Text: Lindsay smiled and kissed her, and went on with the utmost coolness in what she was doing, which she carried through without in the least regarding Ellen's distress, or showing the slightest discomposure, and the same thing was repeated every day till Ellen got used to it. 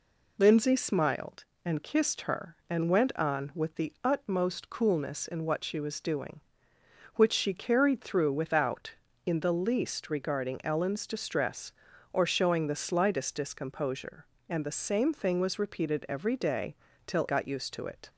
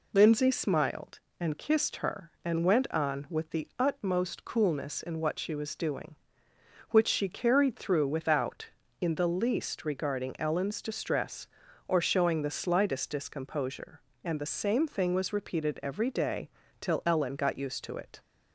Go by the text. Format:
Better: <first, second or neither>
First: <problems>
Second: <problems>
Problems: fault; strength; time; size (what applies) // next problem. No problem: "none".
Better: second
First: pauses between "day" and "till"; slight; at 16.7 s; 0.32 s long // skips "Ellen"; at 17.2 s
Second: pauses between "day" and "till"; slight; at 16.4 s; 0.32 s long